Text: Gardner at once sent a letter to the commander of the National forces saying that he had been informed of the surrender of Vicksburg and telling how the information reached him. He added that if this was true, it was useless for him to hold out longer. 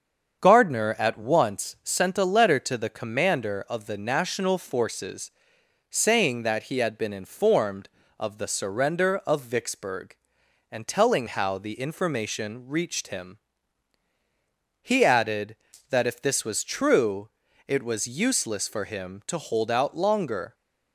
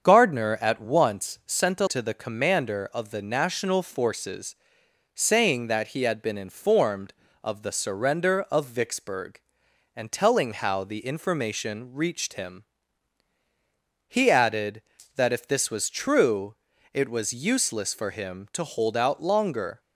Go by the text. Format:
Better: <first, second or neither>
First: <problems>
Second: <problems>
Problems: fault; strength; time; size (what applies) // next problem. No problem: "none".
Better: first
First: starts louder than the rest; strong; until 1.4 s; 7 dB // pauses between "forces" and "saying"; noticeable; at 5.3 s; 0.58 s long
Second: starts louder than the rest; strong; until 1.0 s; 7 dB // skips "letter"; at 1.8 s // pauses between "forces" and "saying"; noticeable; at 4.5 s; 0.58 s long